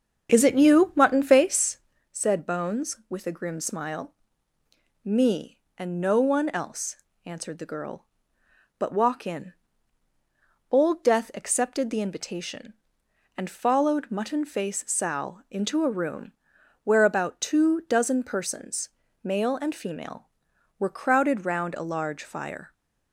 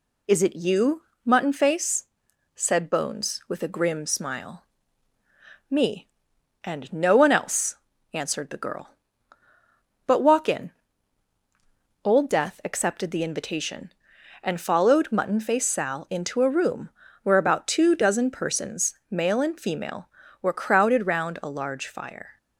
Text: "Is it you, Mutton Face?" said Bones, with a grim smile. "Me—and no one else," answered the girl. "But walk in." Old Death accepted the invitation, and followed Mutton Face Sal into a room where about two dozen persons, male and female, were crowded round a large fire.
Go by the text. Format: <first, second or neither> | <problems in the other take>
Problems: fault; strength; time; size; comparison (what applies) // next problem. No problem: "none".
second | starts louder than the rest; strong; until 2.1 s; 7 dB // pauses between "room" and "where"; noticeable; at 16.3 s; 0.54 s long; slight in the second